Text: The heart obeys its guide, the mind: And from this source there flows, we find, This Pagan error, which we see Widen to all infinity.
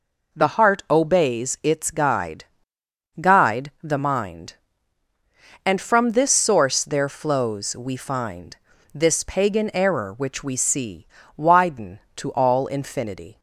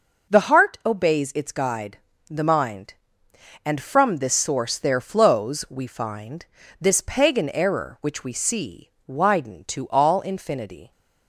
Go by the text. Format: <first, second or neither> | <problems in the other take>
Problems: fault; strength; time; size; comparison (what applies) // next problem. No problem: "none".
second | says "guide" twice; at 3.1 s // pauses between "see" and "Widen"; slight; at 11.0 s; 0.28 s long; slight in the second